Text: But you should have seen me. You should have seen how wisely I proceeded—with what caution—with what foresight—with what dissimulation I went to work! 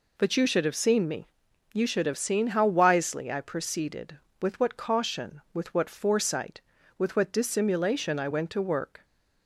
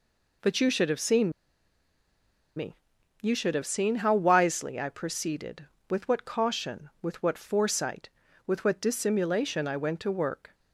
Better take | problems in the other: first | pauses between "seen" and "me"; strong; at 1.3 s; 1.2 s long

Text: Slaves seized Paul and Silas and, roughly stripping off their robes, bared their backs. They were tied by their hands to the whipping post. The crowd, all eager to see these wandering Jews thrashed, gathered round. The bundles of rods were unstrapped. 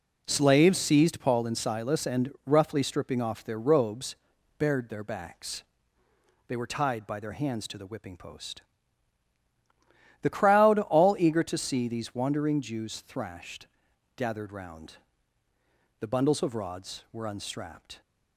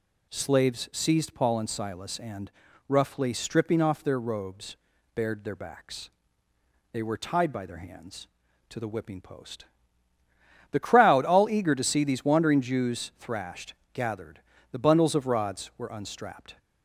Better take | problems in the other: first | skips "round"; at 14.5 s

